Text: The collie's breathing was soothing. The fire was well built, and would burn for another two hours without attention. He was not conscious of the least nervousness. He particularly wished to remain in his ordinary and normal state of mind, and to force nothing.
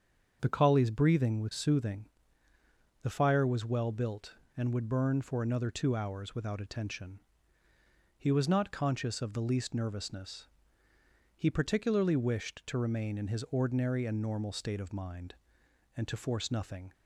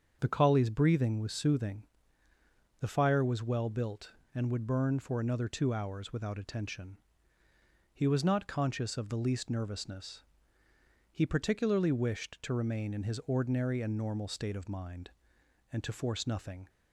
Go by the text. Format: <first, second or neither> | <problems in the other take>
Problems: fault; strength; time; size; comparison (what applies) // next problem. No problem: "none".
neither | starts louder than the rest; the same in both